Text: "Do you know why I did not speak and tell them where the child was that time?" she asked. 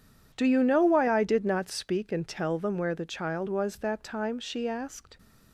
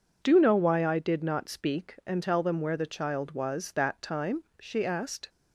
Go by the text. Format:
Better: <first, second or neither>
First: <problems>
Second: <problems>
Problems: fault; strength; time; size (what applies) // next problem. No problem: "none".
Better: first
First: none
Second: skips "you"; at 0.3 s